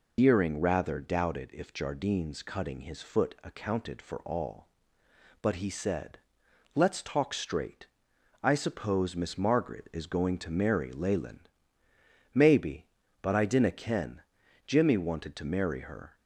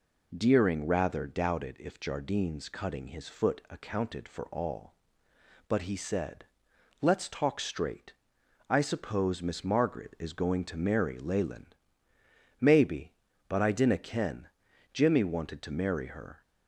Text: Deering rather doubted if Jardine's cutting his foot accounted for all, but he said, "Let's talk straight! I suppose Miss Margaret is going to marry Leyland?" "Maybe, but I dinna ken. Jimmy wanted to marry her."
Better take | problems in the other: second | loses the start of "Deering"; at 0.1 s; 125 ms

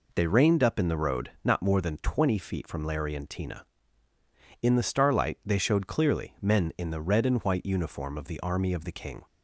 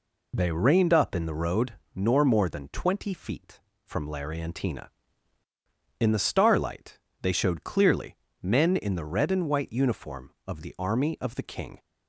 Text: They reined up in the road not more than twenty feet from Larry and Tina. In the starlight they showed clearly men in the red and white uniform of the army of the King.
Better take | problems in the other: first | says "nor" for "not"; at 1.9 s // pauses between "starlight" and "they"; slight; at 6.9 s; 0.22 s long // pauses between "clearly" and "men"; slight; at 8.1 s; 0.26 s long

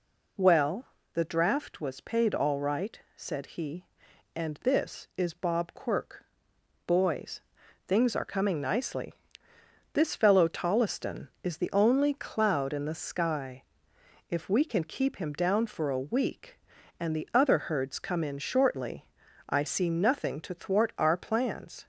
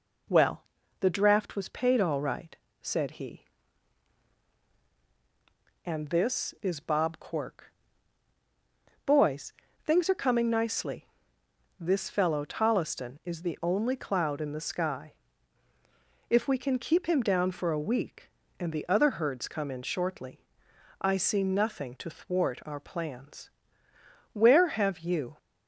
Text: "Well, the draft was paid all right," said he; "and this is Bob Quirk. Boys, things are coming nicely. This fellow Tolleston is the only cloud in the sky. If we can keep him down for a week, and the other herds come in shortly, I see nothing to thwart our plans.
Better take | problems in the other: first | goes on to say "Where have you"; noticeable; from 24.3 s on; 1.0 s long

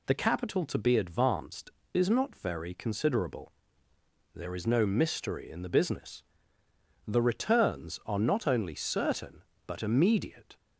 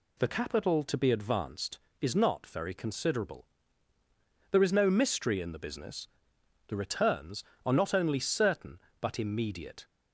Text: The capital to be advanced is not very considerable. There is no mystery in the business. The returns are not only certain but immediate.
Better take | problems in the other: neither | none

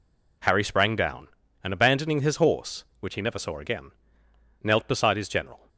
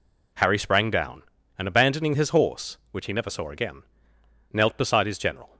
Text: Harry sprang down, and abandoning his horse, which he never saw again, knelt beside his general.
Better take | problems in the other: neither | none

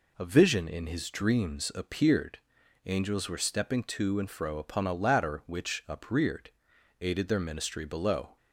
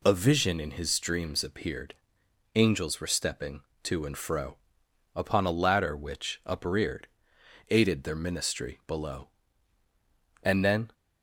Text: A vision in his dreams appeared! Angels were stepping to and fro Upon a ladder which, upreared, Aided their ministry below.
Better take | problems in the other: first | pauses between "fro" and "Upon"; noticeable; at 4.5 s; 0.58 s long // goes on to say "And then"; from 10.4 s on; 0.50 s long

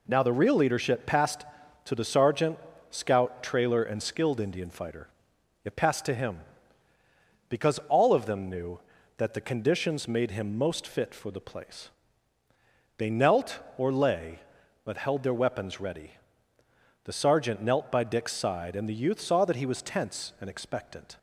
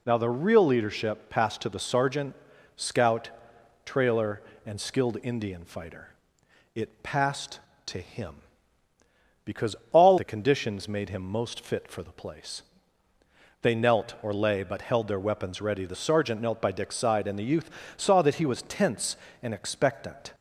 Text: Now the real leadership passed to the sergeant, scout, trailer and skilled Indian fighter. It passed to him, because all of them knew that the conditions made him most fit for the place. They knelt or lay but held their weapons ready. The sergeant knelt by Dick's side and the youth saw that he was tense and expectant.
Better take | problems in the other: first | pauses between "because" and "all"; slight; at 9.7 s; 0.16 s long // skips "of them knew that"; at 10.1 s // pauses between "youth" and "saw"; slight; at 17.7 s; 0.26 s long

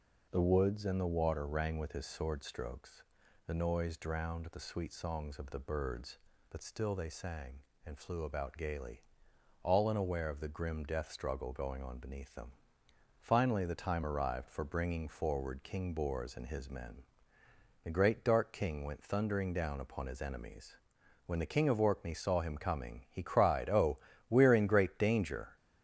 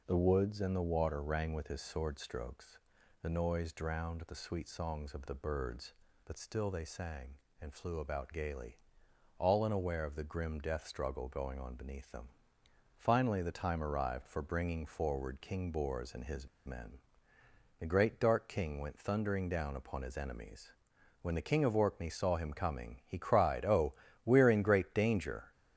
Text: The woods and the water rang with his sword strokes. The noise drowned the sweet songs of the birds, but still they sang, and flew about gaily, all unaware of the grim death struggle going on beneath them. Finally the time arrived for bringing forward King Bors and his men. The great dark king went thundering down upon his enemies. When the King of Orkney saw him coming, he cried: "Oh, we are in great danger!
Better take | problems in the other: first | pauses between "his" and "men"; slight; at 16.4 s; 0.19 s long

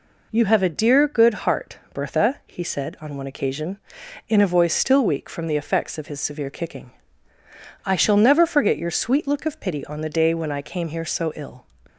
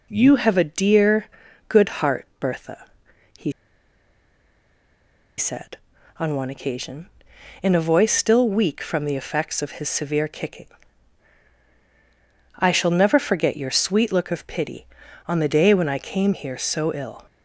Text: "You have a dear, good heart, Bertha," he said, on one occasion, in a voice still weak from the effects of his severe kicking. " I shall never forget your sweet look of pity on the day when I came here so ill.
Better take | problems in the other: first | pauses between "he" and "said"; strong; at 3.5 s; 1.8 s long

